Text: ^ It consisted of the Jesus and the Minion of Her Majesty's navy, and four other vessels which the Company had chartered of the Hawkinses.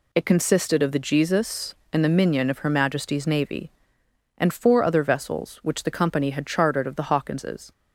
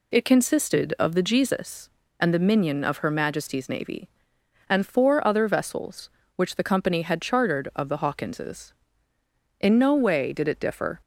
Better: first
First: none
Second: goes on to say "In no way did it differ"; from 9.5 s on; 1.4 s long

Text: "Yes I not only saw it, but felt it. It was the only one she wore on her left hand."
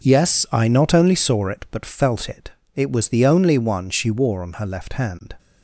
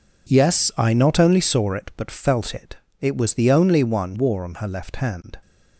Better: first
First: none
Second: skips "she"; at 4.1 s

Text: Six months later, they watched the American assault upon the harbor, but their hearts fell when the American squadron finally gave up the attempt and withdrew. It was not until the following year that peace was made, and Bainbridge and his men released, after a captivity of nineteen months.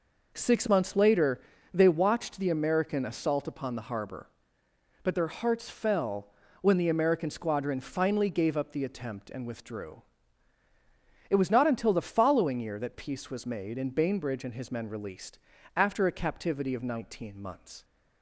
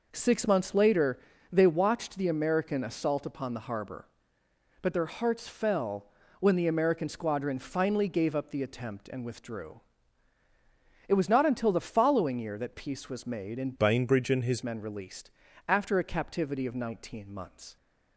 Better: first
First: pauses between "fell" and "when"; slight; at 6.2 s; 0.34 s long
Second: pauses between "fell" and "when"; slight; at 6.0 s; 0.34 s long // changes voice from "Bainbridge" to "his"; from 13.7 to 14.6 s; 0.9 s long

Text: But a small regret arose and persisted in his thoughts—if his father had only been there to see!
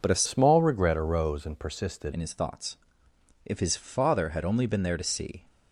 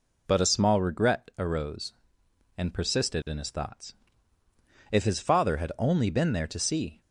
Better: second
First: changes voice from "small" to "persisted"; from 0.2 to 2.1 s; 1.9 s long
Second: none

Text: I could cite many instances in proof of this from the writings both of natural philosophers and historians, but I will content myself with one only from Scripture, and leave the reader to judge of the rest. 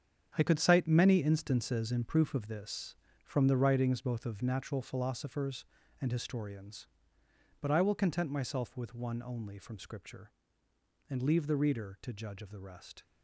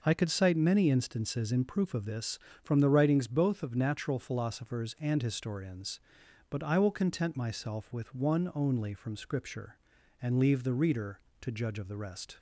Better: second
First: gets quieter; strong; throughout; 10.5 dB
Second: none

